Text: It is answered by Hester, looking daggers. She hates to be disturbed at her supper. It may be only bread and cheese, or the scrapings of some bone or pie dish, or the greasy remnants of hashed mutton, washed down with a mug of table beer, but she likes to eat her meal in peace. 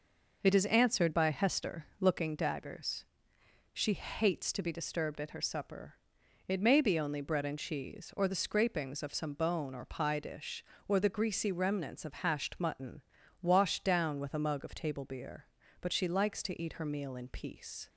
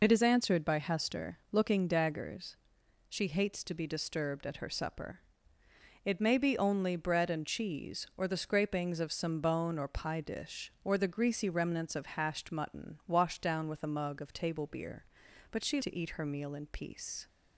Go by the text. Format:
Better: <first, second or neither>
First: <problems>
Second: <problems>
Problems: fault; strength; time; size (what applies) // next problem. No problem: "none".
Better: first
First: none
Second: skips "likes"; at 15.7 s